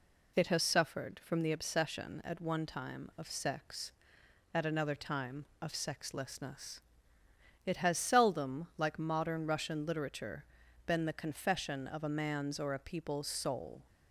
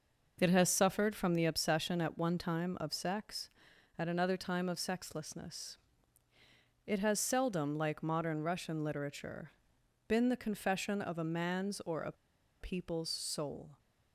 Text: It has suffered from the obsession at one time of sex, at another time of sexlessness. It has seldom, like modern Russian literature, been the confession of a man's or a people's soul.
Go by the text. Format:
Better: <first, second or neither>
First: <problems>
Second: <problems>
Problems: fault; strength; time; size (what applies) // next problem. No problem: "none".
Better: first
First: none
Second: pauses between "a" and "people's"; noticeable; at 12.1 s; 0.47 s long